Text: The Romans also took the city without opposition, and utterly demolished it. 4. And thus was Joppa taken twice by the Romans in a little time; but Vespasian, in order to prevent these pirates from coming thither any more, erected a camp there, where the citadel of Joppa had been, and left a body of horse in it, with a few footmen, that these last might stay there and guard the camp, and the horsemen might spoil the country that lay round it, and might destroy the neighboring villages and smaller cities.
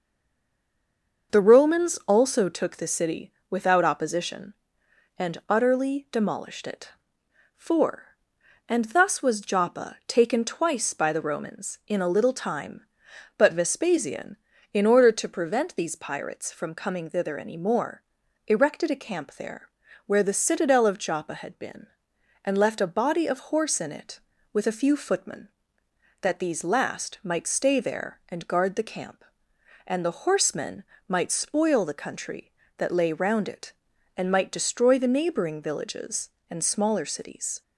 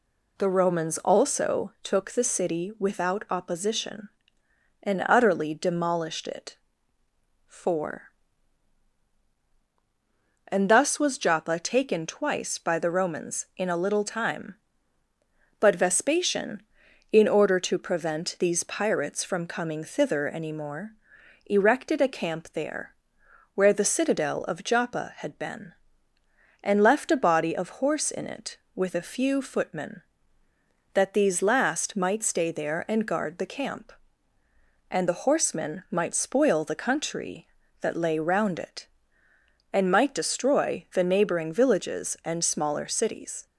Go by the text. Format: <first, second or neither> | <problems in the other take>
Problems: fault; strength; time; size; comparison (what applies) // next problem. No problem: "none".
second | stays silent before the first word; noticeable; until 1.3 s; 1.3 s long // starts louder than the rest; until 2.4 s; 6 dB // pauses between "city" and "without"; slight; at 3.3 s; 0.18 s long // pauses between "horsemen" and "might"; slight; at 30.8 s; 0.24 s long